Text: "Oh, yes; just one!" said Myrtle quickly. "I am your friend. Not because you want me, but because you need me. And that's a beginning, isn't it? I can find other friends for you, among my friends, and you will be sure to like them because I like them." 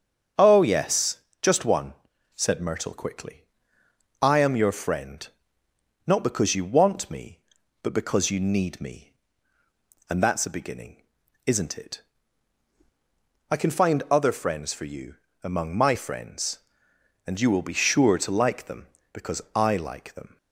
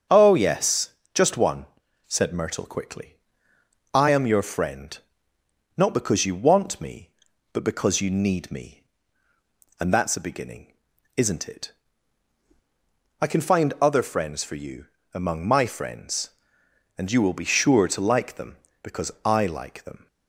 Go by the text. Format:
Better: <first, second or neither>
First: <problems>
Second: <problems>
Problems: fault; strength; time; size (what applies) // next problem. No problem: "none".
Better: neither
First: starts louder than the rest; strong; until 1.6 s; 7.5 dB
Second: starts louder than the rest; strong; until 1.3 s; 7 dB